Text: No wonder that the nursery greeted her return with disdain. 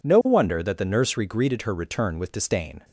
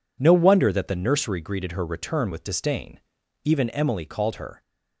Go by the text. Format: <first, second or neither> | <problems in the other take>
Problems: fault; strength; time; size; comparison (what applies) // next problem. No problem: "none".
first | goes on to say "Even Emily called her"; noticeable; from 3.4 s on; 1.1 s long